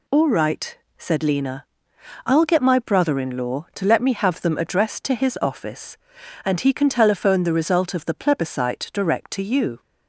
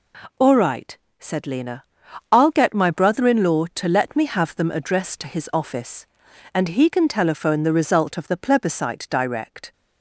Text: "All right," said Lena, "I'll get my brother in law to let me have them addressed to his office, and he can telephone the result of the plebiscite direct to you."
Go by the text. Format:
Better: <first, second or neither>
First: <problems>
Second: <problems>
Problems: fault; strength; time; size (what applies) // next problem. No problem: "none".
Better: first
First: none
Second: stops before "to you"; at 9.7 s